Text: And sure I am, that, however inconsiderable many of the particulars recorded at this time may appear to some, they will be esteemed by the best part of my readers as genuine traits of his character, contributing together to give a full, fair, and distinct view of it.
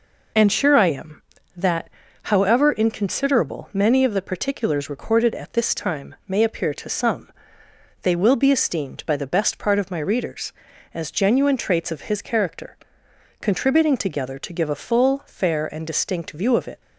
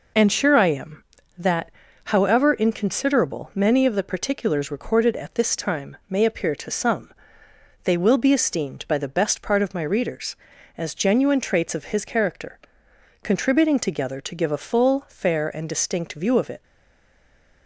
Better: first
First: none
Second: stays silent after the last word; from 16.6 s on; 1.0 s long

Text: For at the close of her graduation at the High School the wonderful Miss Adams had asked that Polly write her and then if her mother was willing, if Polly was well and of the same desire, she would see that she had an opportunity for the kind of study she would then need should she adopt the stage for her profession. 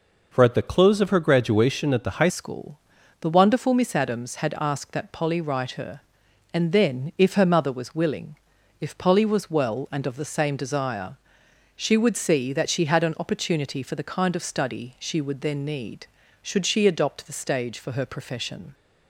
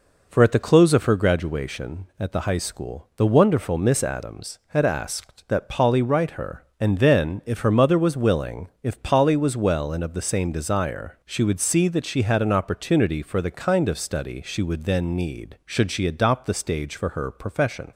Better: second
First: changes voice at "School"; from 2.2 s on; 16.5 s long // pauses between "School" and "the"; at 2.7 s; 0.44 s long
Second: none

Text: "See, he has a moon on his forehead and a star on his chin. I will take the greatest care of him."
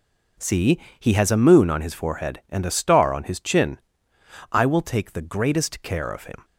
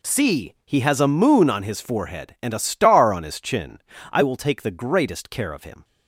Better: neither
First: none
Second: none

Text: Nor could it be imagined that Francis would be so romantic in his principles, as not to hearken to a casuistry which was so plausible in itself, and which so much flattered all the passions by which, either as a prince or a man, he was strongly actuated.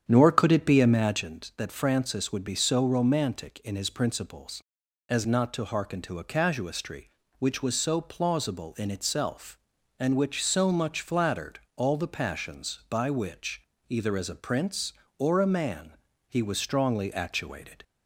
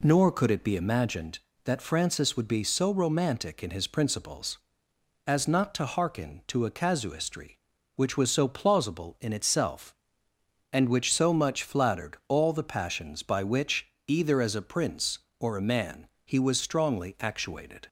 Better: second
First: starts louder than the rest; strong; until 1.4 s; 9 dB // pauses between "flattered" and "all"; slight; at 11.5 s; 0.16 s long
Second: none

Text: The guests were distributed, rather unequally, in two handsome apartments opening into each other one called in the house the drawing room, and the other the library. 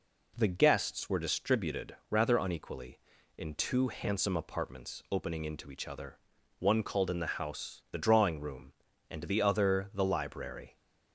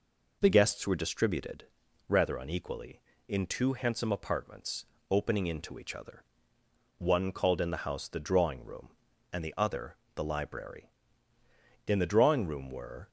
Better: first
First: pauses between "other" and "one"; at 6.1 s; 0.40 s long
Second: pauses between "apartments" and "opening"; slight; at 4.8 s; 0.26 s long // pauses between "other" and "one"; noticeable; at 6.2 s; 0.76 s long // pauses between "other" and "the"; slight; at 9.9 s; 0.20 s long // goes on to say "In the drawing room were"; noticeable; from 11.8 s on; 1.2 s long

